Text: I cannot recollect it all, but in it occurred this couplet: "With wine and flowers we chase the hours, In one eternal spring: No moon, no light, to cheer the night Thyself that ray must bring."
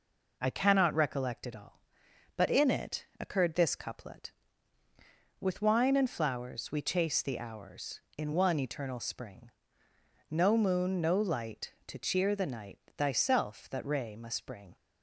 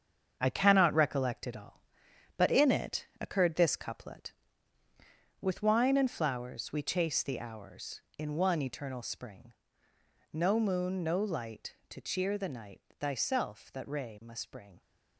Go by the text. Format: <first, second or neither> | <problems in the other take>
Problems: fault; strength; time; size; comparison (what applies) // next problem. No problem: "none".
first | gets quieter; strong; throughout; 7.5 dB // pauses between "it" and "occurred"; slight; at 3.0 s; 0.16 s long; slight in the first // pauses between "night" and "Thyself"; slight; at 12.8 s; 0.18 s long; slight in the first